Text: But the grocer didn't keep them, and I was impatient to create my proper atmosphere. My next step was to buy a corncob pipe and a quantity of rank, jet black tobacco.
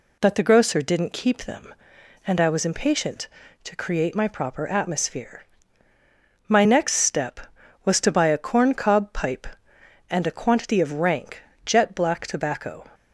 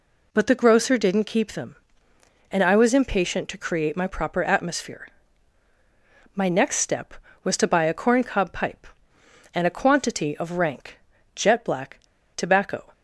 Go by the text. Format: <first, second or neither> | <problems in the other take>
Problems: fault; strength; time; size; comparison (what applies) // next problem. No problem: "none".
first | pauses between "black" and "tobacco"; at 11.9 s; 0.37 s long